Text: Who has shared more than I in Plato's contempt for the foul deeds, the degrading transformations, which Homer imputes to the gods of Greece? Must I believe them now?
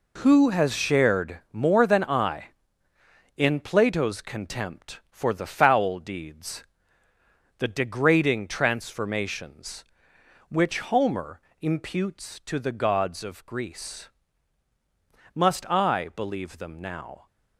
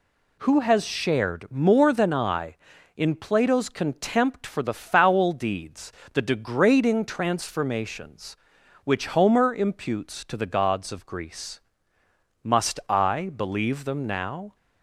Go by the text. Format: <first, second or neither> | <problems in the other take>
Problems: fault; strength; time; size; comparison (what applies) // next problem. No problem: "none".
second | gets quieter; strong; throughout; 9 dB // pauses between "Homer" and "imputes"; slight; at 11.4 s; 0.20 s long